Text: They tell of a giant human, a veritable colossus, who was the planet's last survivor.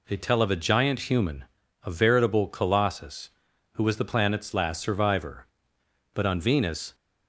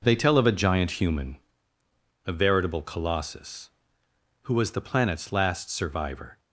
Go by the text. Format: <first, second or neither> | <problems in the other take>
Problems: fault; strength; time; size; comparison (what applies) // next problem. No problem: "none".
second | goes on to say "But on Venus"; noticeable; from 6.1 s on; 0.82 s long